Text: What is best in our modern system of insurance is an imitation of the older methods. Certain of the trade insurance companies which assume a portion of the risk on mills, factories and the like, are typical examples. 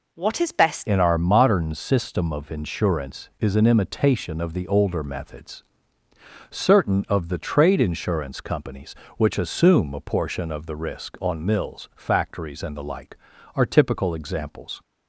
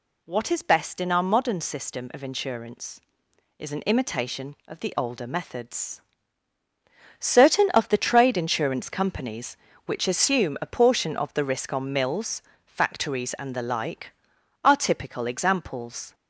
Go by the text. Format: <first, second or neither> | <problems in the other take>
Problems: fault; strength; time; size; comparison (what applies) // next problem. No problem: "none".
second | changes voice at "in"; from 0.8 s on; 14.0 s long